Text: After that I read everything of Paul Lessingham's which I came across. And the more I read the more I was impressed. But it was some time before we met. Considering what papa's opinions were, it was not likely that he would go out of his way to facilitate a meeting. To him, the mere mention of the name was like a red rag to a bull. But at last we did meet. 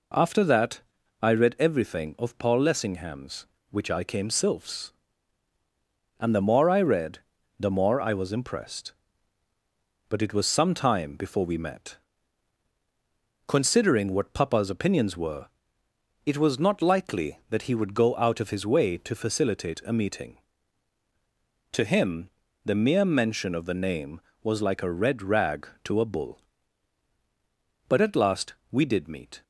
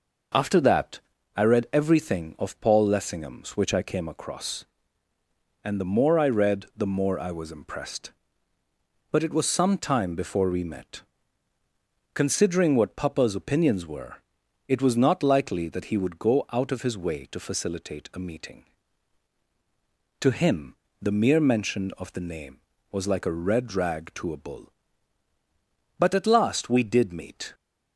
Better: second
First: pauses between "that" and "I"; at 0.8 s; 0.42 s long // says "sylphs" for "across"; at 4.2 s // pauses between "read" and "the"; at 7.1 s; 0.40 s long // pauses between "last" and "we"; slight; at 28.5 s; 0.16 s long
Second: pauses between "that" and "I"; at 0.9 s; 0.38 s long

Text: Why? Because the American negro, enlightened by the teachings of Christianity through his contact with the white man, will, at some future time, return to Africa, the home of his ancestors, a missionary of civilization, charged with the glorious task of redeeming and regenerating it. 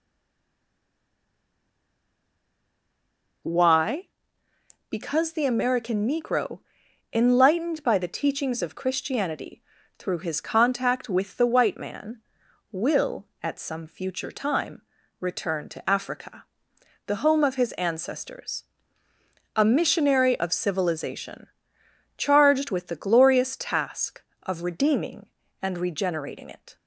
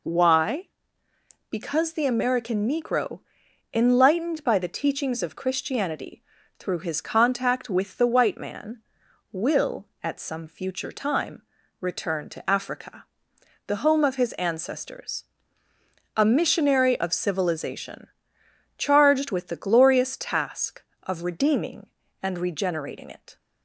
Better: second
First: stays silent before the first word; strong; until 3.4 s; 3.4 s long // pauses between "Christianity" and "through"; slight; at 9.6 s; 0.36 s long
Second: pauses between "Christianity" and "through"; slight; at 6.2 s; 0.36 s long

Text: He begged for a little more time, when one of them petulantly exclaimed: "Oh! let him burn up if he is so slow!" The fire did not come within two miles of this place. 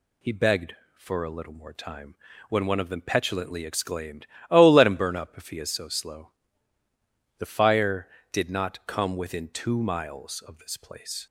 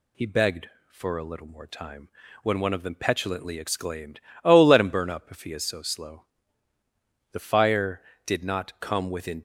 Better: first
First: none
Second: stops before "two miles of this place"; at 9.3 s

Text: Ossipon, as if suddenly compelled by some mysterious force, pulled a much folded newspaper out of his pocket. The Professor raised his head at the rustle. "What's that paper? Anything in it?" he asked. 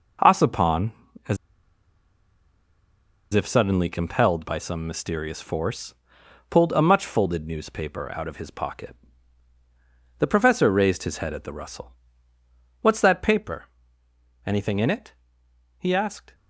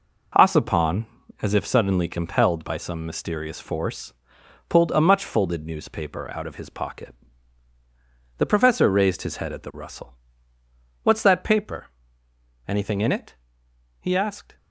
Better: second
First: pauses between "as" and "if"; strong; at 1.3 s; 1.9 s long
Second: none

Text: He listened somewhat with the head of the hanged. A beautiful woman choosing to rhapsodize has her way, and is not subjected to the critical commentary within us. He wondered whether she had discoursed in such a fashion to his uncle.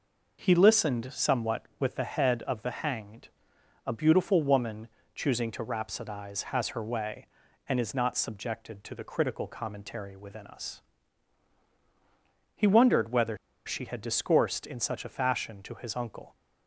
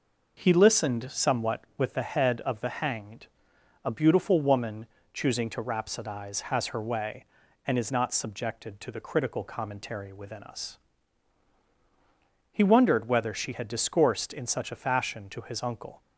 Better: second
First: pauses between "woman" and "choosing"; slight; at 4.8 s; 0.26 s long // pauses between "whether" and "she"; slight; at 13.3 s; 0.30 s long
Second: pauses between "woman" and "choosing"; slight; at 4.8 s; 0.26 s long

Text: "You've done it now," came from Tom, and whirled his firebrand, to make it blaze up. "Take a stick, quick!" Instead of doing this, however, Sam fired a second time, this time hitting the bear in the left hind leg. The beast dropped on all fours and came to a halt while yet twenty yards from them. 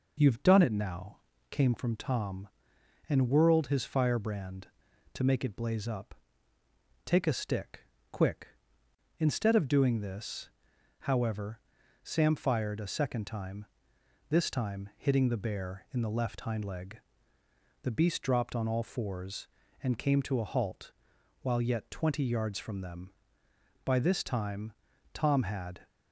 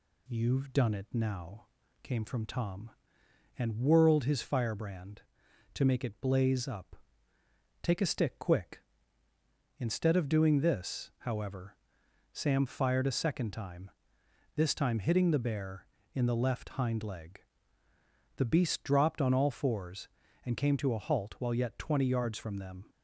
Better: second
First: pauses between "halt" and "while"; noticeable; at 20.9 s; 0.50 s long // goes on to say "By this time Tom had"; strong; from 23.8 s on; 2.0 s long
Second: none

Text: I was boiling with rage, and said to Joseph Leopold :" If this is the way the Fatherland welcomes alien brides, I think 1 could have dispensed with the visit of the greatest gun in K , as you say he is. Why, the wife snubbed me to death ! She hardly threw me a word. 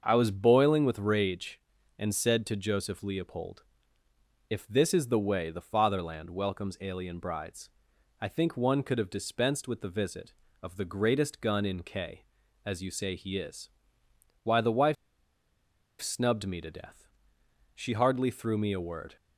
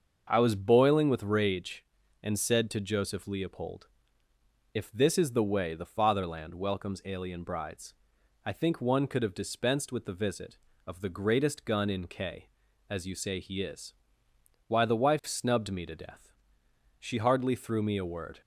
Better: second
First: starts louder than the rest; until 1.0 s; 7 dB // pauses between "wife" and "snubbed"; at 14.9 s; 1.0 s long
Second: starts louder than the rest; until 1.3 s; 6.5 dB

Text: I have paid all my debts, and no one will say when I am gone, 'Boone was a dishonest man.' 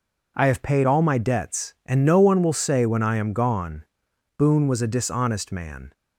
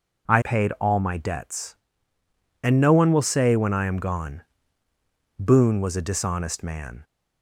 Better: first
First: none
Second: skips "have"; at 0.4 s

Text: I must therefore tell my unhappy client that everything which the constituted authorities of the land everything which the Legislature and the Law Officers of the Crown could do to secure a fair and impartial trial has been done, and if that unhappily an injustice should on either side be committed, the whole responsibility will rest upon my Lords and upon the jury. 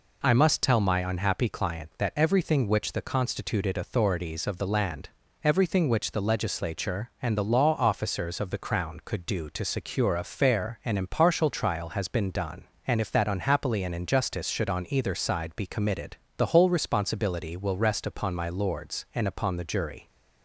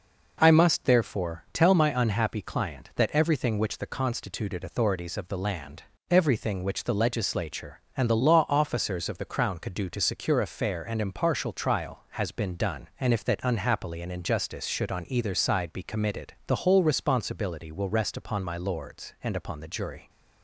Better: second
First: skips "therefore"; at 0.6 s // pauses between "land" and "everything"; slight; at 5.0 s; 0.34 s long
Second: pauses between "land" and "everything"; slight; at 5.8 s; 0.26 s long

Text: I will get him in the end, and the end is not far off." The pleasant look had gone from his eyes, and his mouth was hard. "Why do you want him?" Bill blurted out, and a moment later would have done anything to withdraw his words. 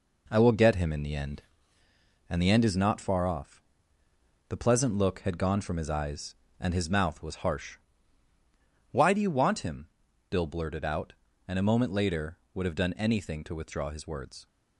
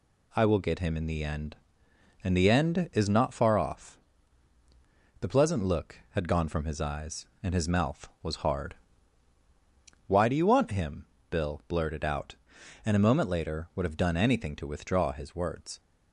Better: second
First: says "harsh" for "hard"; at 7.4 s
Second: none

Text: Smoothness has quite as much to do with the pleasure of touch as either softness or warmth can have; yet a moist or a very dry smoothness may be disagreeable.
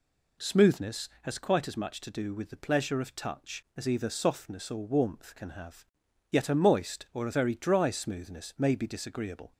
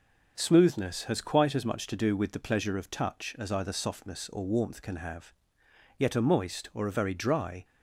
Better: first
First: none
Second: stops before "smoothness may be disagreeable"; at 7.6 s

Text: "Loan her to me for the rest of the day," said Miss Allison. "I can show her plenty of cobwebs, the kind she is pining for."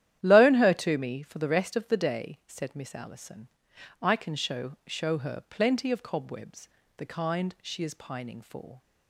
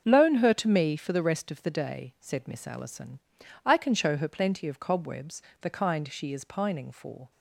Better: second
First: starts louder than the rest; strong; until 1.2 s; 11.5 dB // says "show" twice; at 4.8 s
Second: starts louder than the rest; until 1.0 s; 6.5 dB

